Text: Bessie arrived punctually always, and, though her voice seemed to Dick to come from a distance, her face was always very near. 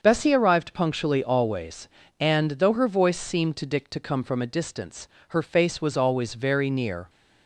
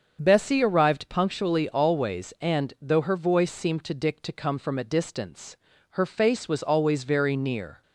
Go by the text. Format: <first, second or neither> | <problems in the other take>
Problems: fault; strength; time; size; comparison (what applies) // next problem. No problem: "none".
neither | starts louder than the rest; the same in both